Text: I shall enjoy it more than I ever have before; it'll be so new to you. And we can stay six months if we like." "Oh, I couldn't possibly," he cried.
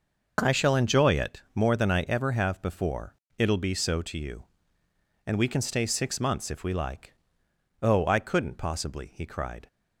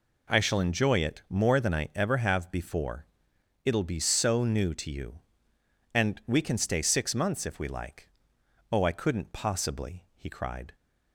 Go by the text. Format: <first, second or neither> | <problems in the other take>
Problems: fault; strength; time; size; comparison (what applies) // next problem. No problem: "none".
second | skips "new"; at 4.0 s